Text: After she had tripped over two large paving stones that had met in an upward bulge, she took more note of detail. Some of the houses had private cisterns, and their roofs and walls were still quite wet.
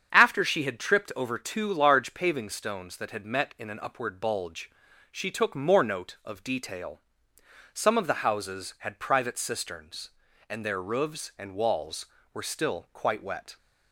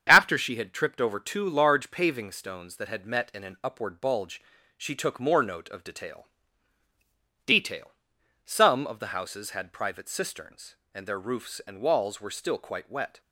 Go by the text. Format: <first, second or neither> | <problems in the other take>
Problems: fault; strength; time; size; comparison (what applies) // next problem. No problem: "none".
first | starts louder than the rest; strong; until 1.0 s; 8 dB; strong in the first // says "detail" twice; at 7.4 s